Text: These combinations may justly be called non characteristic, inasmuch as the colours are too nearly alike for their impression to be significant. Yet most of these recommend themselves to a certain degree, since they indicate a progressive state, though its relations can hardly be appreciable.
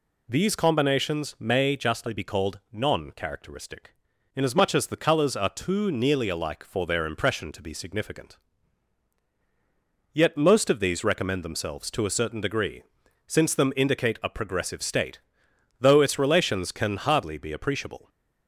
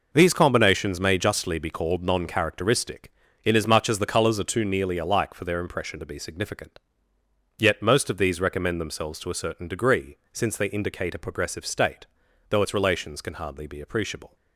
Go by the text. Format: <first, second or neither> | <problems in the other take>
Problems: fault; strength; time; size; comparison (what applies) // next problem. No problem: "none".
second | says "them" for "they"; at 13.5 s